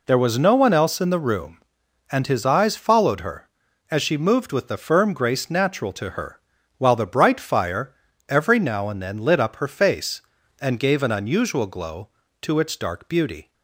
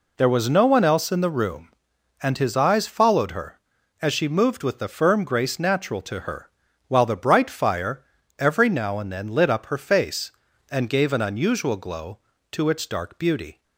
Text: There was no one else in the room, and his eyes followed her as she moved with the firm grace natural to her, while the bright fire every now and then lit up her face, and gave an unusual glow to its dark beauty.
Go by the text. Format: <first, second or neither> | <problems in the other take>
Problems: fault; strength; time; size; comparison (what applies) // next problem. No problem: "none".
neither | pauses between "fire" and "every"; slight; the same in both